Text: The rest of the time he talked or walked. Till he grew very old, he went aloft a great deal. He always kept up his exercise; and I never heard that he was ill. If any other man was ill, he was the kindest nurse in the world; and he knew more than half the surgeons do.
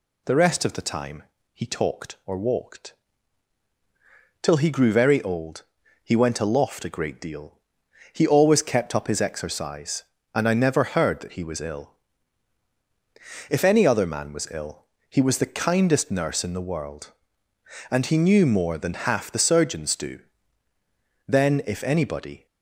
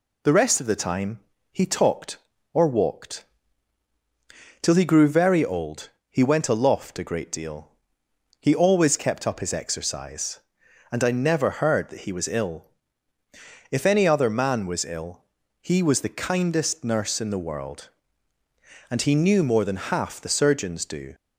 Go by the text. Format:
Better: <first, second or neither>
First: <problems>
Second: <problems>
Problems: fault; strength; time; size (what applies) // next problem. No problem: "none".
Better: second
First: pauses between "time" and "he"; slight; at 1.2 s; 0.28 s long // goes on to say "Then if anybody"; noticeable; from 21.2 s on; 1.1 s long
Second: pauses between "time" and "he"; slight; at 1.2 s; 0.32 s long